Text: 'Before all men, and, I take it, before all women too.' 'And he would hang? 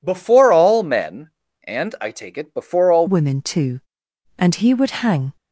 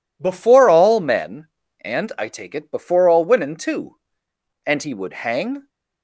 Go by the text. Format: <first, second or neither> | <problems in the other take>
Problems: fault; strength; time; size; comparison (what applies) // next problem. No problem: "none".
second | changes voice at "women"; from 3.0 s on; 2.3 s long